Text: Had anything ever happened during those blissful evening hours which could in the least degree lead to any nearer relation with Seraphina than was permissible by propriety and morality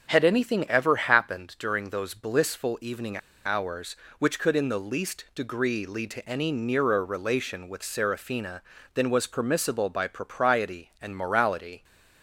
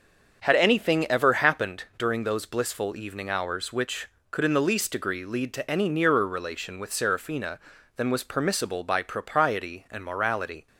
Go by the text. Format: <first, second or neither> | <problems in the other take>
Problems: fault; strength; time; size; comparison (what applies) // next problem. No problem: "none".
second | starts louder than the rest; until 1.1 s; 7 dB; also in the second // pauses between "evening" and "hours"; slight; at 3.1 s; 0.26 s long